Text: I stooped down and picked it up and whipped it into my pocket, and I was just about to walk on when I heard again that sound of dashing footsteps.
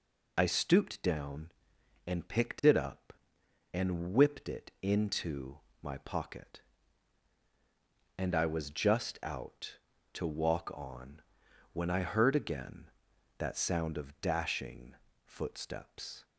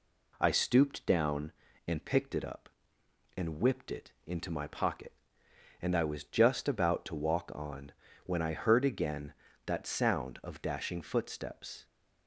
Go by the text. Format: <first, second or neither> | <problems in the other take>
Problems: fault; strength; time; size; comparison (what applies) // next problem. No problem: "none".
second | pauses between "into" and "my"; slight; at 5.5 s; 0.22 s long // says "out" for "about"; at 9.2 s // pauses between "on" and "when"; noticeable; at 11.2 s; 0.50 s long; slight in the second // pauses between "dashing" and "footsteps"; slight; at 14.9 s; 0.30 s long